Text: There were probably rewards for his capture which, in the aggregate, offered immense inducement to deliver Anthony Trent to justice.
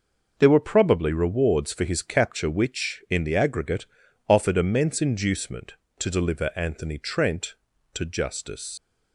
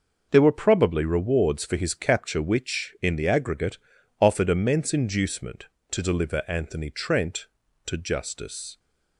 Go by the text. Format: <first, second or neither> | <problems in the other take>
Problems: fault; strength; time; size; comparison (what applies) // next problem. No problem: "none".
second | leaves "justice" unfinished; at 8.7 s; 90 ms